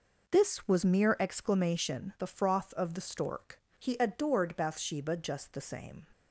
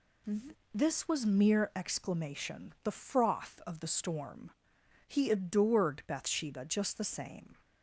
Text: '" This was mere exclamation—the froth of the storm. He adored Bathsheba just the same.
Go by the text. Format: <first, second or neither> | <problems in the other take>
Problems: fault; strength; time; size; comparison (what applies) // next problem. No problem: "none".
second | says "stork" for "storm"; at 3.0 s